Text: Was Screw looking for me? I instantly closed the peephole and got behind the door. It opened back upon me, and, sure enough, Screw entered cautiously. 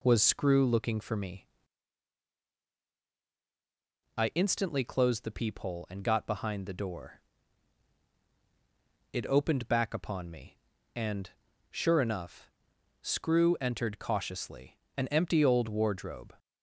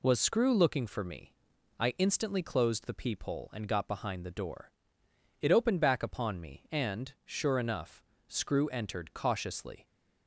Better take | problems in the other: second | goes on to say "An empty old wardrobe"; from 14.9 s on; 1.3 s long

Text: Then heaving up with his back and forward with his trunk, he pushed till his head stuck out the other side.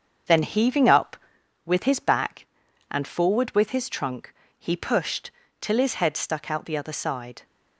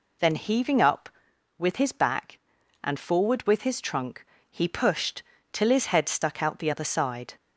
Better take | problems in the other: second | gets quieter; noticeable; throughout; 5.5 dB // pauses between "pushed" and "till"; slight; at 5.3 s; 0.28 s long; slight in the second

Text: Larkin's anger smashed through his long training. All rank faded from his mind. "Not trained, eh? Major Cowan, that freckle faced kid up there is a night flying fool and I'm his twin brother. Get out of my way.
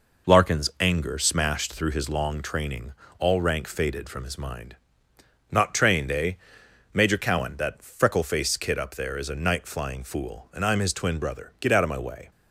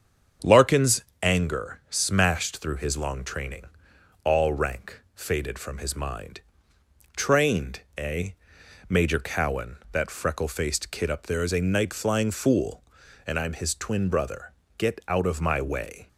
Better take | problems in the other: first | starts louder than the rest; strong; until 1.6 s; 7.5 dB // pauses between "Larkin's" and "anger"; slight; at 1.0 s; 0.18 s long // skips "Not"; at 6.7 s

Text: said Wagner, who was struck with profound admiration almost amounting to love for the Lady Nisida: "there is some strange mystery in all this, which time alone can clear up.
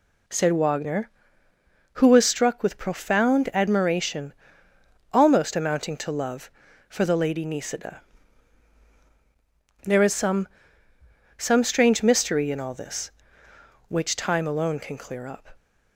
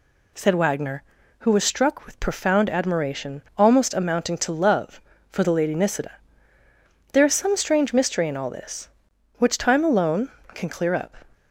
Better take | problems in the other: second | pauses between "admiration" and "almost"; noticeable; at 4.3 s; 0.80 s long; slight in the second // says "some" twice; at 11.3 s

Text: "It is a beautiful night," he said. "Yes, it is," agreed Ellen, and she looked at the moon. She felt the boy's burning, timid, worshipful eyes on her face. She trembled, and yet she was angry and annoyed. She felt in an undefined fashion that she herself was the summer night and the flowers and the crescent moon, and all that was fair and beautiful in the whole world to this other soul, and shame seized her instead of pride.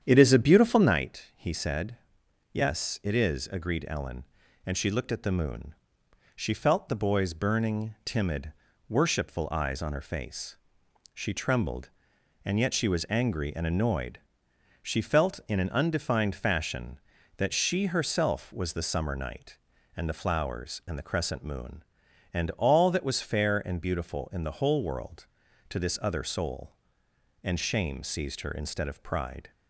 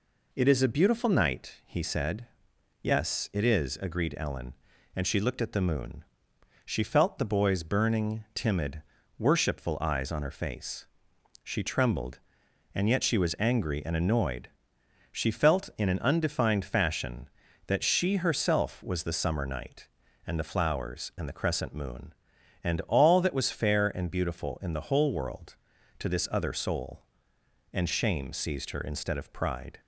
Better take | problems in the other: second | starts louder than the rest; strong; until 0.9 s; 9 dB

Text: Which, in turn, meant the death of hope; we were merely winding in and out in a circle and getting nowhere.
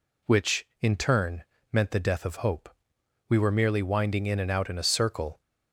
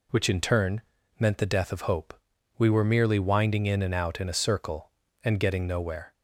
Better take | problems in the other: second | stops before "and getting nowhere"; at 5.4 s

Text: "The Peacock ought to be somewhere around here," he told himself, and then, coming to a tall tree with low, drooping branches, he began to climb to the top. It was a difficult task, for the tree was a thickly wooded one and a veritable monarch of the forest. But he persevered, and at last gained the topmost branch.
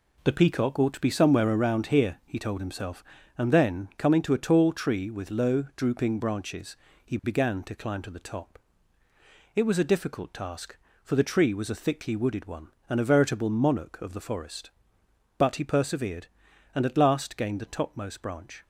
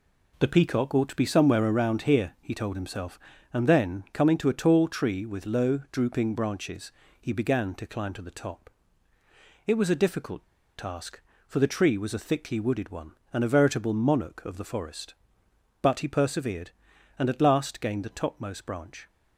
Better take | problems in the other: first | pauses between "difficult" and "task"; slight; at 10.4 s; 0.33 s long

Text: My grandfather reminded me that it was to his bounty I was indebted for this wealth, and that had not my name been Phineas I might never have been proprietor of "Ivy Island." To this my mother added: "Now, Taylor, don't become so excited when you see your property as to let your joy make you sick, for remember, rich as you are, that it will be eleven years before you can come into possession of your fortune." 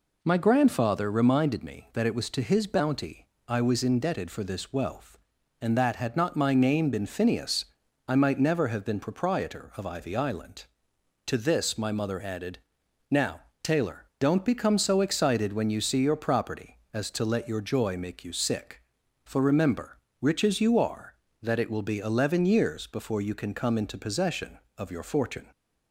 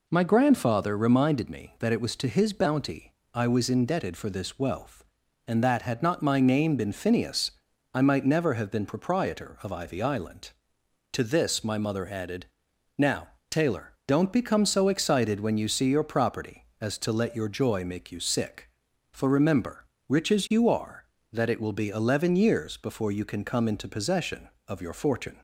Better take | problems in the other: neither | pauses between "bounty" and "I"; slight; the same in both // pauses between "Phineas" and "I"; the same in both

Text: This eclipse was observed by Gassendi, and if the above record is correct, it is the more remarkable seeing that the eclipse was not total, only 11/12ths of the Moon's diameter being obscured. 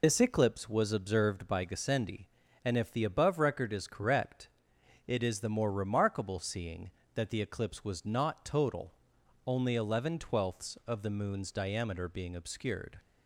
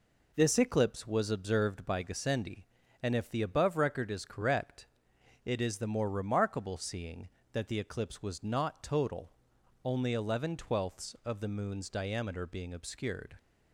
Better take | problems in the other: second | loses the start of "This"; at 0.0 s; 70 ms

